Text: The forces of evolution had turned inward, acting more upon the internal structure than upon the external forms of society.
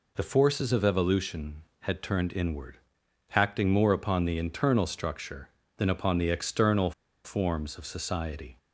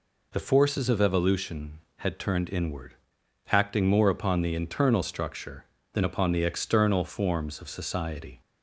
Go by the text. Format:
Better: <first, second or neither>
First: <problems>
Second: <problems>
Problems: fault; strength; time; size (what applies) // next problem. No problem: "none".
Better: second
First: pauses between "external" and "forms"; slight; at 6.9 s; 0.33 s long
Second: none